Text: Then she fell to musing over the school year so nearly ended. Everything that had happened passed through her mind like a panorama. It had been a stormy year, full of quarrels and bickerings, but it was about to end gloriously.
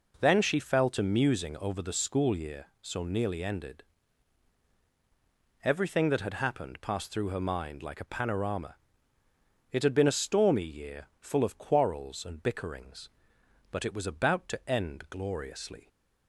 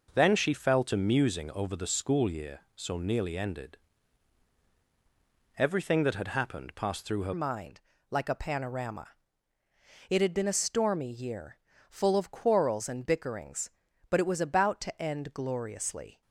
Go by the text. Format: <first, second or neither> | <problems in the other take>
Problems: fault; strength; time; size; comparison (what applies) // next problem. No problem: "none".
first | changes voice at "mind"; from 7.3 s on; 8.9 s long // pauses between "mind" and "like"; slight; at 7.7 s; 0.30 s long